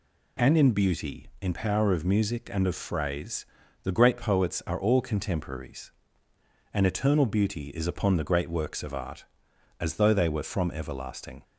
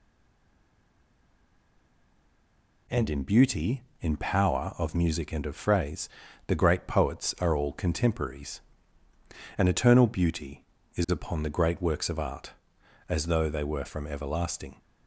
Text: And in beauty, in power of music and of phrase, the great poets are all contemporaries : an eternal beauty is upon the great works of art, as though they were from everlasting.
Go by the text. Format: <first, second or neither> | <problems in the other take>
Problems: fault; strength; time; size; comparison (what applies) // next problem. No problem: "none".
first | stays silent before the first word; strong; until 2.8 s; 2.8 s long